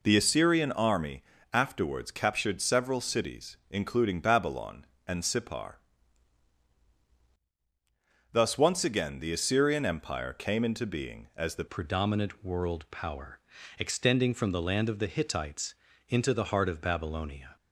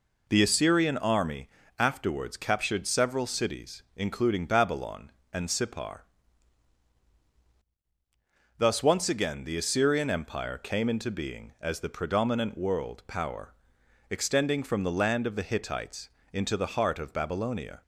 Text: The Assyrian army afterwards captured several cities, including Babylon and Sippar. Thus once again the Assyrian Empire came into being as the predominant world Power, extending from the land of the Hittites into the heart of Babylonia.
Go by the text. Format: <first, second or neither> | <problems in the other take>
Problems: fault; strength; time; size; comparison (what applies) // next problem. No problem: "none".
second | pauses between "army" and "afterwards"; slight; at 1.2 s; 0.28 s long; slight in the second // changes voice at "predominant"; from 11.6 s on; 5.9 s long // pauses between "Hittites" and "into"; slight; at 15.7 s; 0.34 s long; slight in the second